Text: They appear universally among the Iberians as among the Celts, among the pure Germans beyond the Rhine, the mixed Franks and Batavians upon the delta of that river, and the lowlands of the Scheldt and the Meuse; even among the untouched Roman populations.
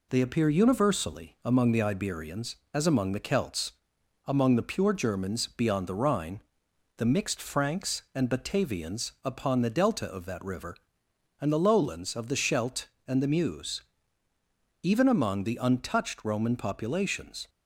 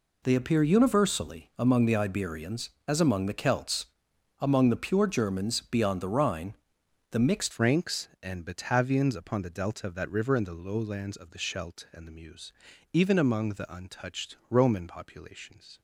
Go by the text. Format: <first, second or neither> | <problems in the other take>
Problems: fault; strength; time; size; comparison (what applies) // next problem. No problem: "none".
first | changes voice at "Franks"; from 7.5 s on; 8.2 s long